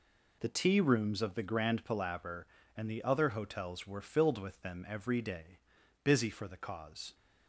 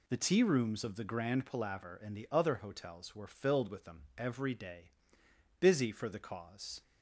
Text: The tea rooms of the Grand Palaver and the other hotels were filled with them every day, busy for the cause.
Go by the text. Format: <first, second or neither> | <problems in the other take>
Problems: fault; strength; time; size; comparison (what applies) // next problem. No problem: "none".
neither | none